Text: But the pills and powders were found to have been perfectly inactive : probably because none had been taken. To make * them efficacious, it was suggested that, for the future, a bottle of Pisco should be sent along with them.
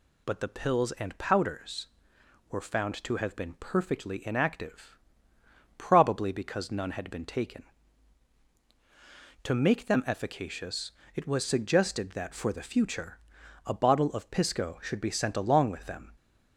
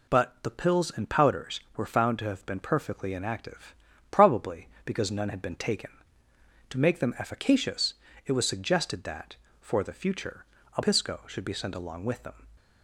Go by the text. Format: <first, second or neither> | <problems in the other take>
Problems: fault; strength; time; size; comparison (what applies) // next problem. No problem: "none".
first | skips "bottle of"; at 10.8 s